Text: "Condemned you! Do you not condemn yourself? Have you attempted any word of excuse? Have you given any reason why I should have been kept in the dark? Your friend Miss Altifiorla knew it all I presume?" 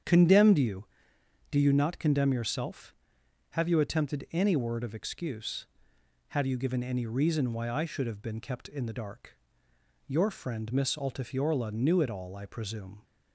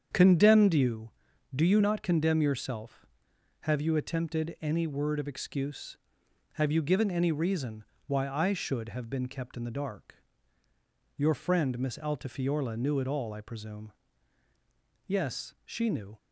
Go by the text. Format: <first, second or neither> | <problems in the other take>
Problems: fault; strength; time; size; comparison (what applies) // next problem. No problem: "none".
first | starts louder than the rest; strong; until 1.5 s; 7.5 dB; strong in the first // pauses between "reason" and "why"; slight; at 7.8 s; 0.22 s long // goes on to say "Yes she knew"; noticeable; from 15.0 s on; 1.1 s long